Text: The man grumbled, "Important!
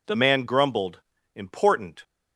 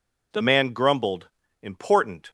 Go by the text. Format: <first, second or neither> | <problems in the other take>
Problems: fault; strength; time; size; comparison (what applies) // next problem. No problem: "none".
neither | none